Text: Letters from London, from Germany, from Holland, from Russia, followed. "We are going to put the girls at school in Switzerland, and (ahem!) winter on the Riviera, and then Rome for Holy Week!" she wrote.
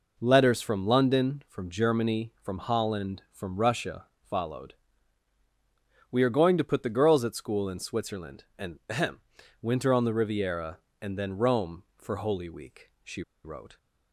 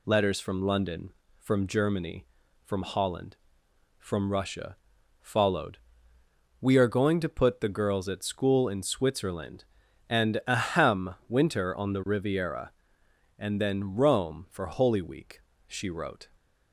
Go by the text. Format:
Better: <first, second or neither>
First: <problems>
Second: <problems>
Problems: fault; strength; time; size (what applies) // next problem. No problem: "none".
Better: second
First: pauses between "she" and "wrote"; slight; at 13.2 s; 0.23 s long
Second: none